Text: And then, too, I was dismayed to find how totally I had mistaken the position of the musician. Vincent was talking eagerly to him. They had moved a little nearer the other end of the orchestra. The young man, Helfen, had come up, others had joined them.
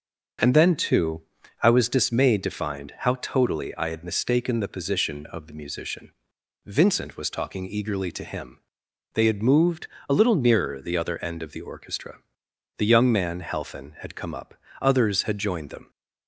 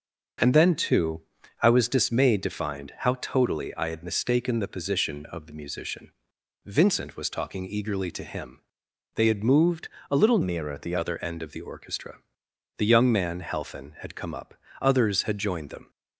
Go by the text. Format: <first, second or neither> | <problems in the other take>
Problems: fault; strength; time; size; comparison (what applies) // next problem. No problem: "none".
first | starts louder than the rest; until 1.8 s; 6.5 dB; also in the first // pauses between "moved" and "a"; slight; at 9.8 s; 0.20 s long; slight in the first // changes voice from "nearer" to "the"; from 10.4 to 10.9 s; 0.5 s long